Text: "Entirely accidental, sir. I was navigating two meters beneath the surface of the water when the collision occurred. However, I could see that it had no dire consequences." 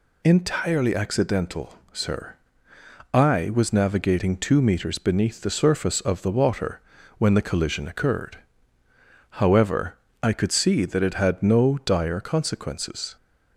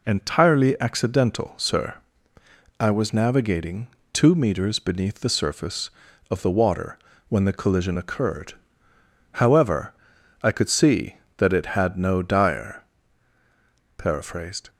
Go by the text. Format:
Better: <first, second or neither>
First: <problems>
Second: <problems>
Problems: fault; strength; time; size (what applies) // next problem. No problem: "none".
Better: first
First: pauses between "water" and "when"; at 6.7 s; 0.38 s long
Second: pauses between "navigating" and "two"; slight; at 3.8 s; 0.24 s long // pauses between "water" and "when"; slight; at 6.9 s; 0.30 s long // says "paraphrased" for "consequences"; at 13.9 s